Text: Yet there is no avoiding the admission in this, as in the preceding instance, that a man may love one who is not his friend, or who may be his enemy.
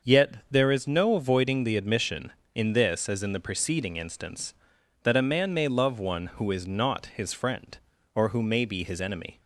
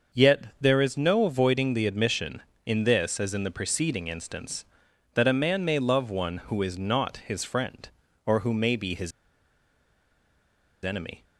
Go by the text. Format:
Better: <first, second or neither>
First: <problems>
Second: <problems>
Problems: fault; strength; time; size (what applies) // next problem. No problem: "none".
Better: first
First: starts louder than the rest; until 1.1 s; 6.5 dB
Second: starts louder than the rest; until 1.2 s; 6.5 dB // pauses between "his" and "enemy"; strong; at 9.1 s; 1.7 s long